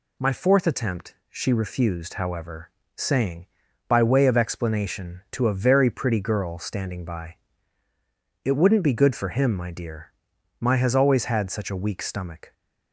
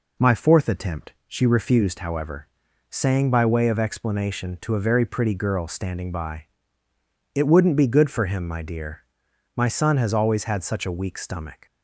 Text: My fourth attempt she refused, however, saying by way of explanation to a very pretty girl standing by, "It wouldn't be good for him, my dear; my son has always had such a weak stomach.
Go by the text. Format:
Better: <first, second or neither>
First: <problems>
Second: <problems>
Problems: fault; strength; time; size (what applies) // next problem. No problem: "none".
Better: second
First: pauses between "attempt" and "she"; slight; at 1.1 s; 0.16 s long // skips "son"; at 10.7 s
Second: pauses between "attempt" and "she"; slight; at 1.1 s; 0.16 s long